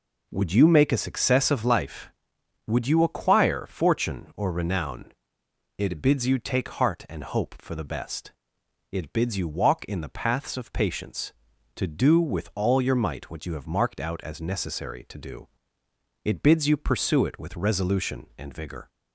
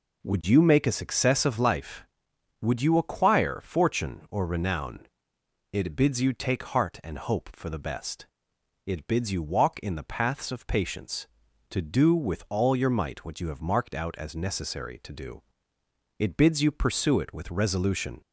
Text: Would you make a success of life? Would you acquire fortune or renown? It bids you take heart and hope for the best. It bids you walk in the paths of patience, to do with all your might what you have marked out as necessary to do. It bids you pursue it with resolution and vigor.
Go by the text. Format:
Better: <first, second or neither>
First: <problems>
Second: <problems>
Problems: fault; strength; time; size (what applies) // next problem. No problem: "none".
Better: first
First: none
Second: stops before "and vigor"; at 18.2 s